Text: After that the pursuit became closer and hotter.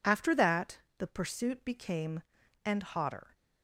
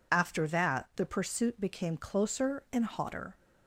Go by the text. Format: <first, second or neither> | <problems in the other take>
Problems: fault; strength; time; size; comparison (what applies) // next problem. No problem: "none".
second | pauses between "that" and "the"; slight; at 0.7 s; 0.18 s long // skips "closer"; at 2.4 s